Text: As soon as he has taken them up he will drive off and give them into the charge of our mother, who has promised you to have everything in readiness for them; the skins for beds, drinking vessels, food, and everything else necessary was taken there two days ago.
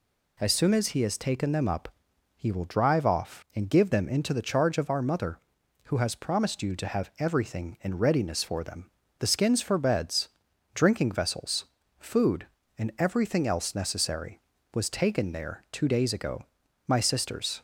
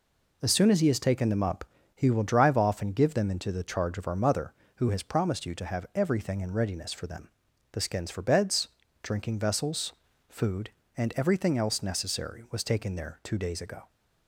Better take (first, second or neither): second